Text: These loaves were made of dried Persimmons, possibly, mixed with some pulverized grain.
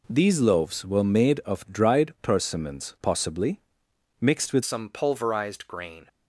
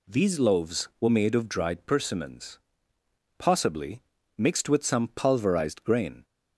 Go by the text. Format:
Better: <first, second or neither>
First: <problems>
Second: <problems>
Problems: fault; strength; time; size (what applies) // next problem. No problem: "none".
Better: second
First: changes voice at "some"; from 4.6 s on; 1.4 s long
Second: none